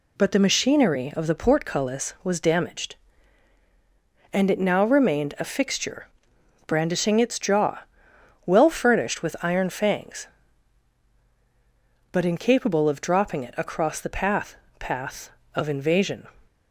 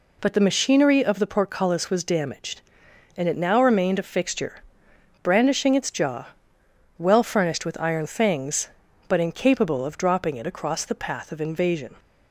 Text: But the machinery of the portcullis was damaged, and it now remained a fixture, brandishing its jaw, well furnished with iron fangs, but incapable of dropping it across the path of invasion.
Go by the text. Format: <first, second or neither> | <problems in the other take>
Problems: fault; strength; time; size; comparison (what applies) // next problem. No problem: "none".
second | says "path" twice; at 14.7 s